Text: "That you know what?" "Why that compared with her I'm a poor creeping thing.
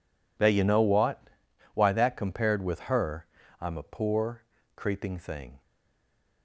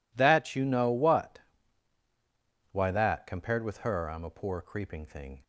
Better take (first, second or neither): second